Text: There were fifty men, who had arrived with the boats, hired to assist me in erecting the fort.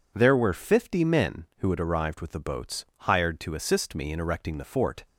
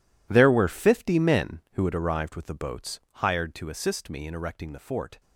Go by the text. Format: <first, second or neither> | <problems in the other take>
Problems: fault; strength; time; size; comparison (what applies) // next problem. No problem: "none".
first | gets quieter; strong; throughout; 16 dB